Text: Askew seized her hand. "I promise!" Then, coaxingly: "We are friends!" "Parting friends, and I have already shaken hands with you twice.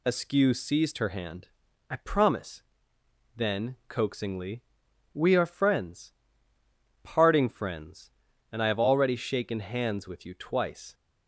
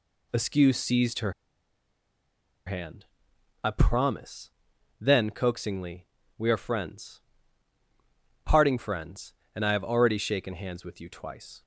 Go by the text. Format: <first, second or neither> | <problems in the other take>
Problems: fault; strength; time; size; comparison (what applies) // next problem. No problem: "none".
first | pauses between "her" and "hand"; strong; at 1.3 s; 1.3 s long